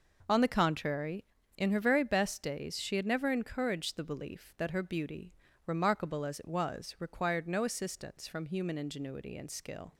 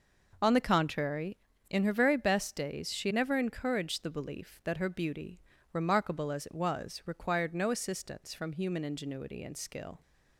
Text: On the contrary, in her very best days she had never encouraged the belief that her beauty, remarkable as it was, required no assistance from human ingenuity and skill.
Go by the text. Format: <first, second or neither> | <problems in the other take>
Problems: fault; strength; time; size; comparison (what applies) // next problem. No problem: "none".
first | skips "had"; at 3.1 s